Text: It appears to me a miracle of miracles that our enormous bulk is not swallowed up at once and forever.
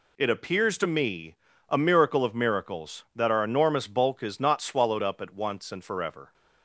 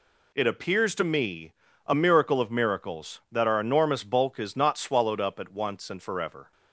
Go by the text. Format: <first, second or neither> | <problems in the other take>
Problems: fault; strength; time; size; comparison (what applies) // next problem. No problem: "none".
neither | pauses between "me" and "a"; slight; the same in both